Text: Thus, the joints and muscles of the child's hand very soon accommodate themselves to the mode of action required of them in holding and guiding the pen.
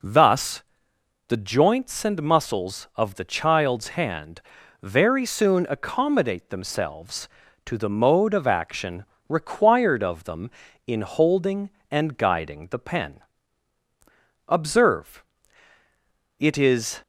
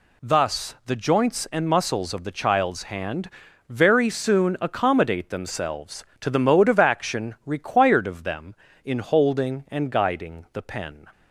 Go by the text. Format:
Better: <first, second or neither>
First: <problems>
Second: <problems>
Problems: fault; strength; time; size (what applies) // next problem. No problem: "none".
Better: second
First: pauses between "hand" and "very"; at 4.4 s; 0.40 s long // pauses between "action" and "required"; slight; at 9.0 s; 0.24 s long // goes on to say "Observe it is"; strong; from 14.4 s on; 2.5 s long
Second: pauses between "hand" and "very"; at 3.2 s; 0.40 s long